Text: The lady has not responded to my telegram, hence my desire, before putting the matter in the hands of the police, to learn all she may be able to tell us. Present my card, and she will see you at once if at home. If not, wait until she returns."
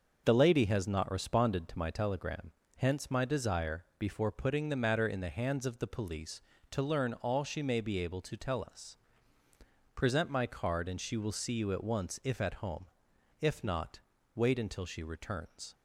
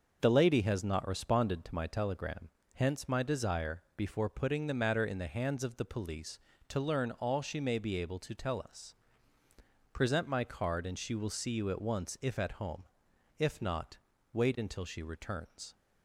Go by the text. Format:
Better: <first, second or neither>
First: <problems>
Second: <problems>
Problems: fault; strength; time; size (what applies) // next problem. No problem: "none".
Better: neither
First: starts louder than the rest; until 1.2 s; 6.5 dB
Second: starts louder than the rest; until 1.2 s; 6 dB